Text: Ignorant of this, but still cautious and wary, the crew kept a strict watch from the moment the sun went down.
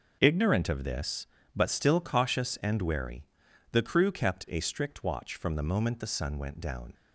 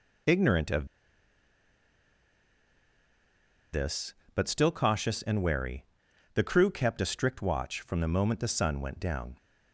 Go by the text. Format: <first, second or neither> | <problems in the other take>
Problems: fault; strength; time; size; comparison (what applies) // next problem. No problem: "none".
first | pauses between "of" and "this"; strong; at 0.8 s; 2.8 s long